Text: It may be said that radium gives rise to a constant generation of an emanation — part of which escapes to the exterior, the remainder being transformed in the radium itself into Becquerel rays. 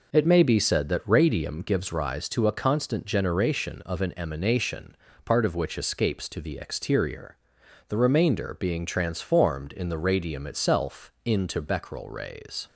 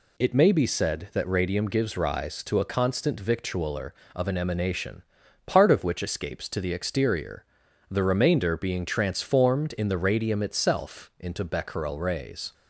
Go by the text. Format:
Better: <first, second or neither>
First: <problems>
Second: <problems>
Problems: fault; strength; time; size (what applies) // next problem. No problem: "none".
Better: first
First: none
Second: says "victualler" for "generation"; at 3.1 s